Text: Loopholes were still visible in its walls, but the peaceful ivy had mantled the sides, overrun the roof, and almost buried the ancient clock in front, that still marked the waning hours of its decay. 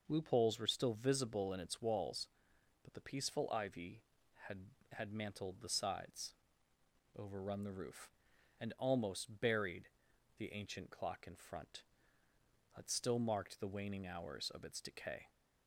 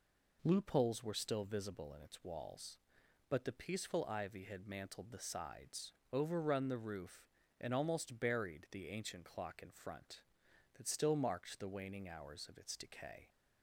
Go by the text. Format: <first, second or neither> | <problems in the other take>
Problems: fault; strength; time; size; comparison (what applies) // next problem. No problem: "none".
second | says "had" twice; at 4.9 s // pauses between "buried" and "the"; noticeable; at 9.8 s; 0.50 s long